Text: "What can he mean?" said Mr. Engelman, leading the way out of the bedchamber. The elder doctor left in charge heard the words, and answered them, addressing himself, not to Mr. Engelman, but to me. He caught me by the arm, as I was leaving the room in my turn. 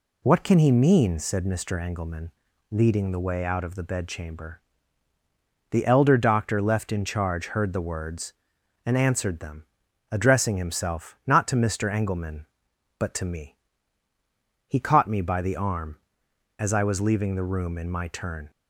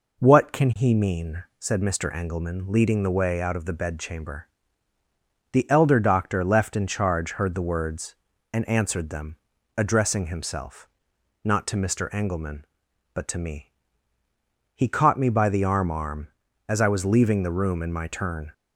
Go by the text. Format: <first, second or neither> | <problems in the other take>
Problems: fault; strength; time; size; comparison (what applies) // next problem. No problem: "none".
first | says "arm" twice; at 15.9 s